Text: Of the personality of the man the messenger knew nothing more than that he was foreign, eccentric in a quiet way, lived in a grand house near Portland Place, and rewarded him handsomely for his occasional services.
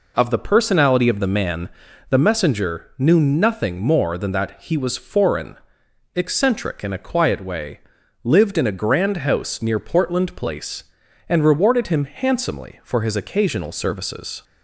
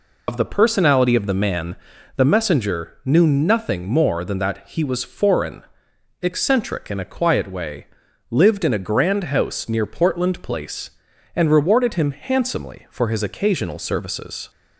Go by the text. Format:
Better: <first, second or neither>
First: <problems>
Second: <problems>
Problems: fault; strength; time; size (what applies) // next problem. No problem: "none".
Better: first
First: pauses between "man" and "the"; at 1.6 s; 0.40 s long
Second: loses the start of "Of"; at 0.2 s; 60 ms // pauses between "man" and "the"; at 1.7 s; 0.40 s long